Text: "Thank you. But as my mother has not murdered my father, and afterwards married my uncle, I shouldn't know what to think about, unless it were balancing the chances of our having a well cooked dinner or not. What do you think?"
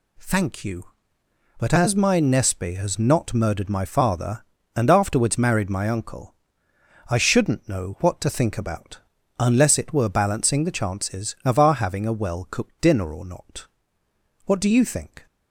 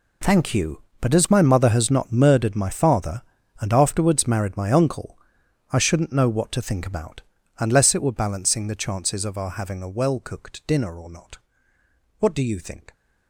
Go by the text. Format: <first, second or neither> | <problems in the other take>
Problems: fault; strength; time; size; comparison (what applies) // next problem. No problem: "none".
second | says "nespe" for "mother"; at 2.1 s